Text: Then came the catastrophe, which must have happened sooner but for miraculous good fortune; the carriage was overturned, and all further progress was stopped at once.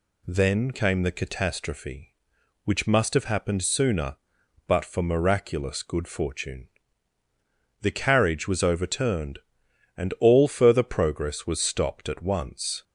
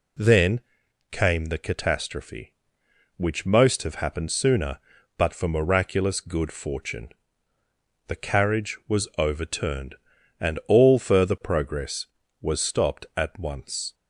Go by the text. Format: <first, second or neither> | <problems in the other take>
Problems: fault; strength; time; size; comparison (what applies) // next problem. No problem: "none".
first | pauses between "Then" and "came"; noticeable; at 0.6 s; 0.50 s long // says "most" for "must"; at 3.4 s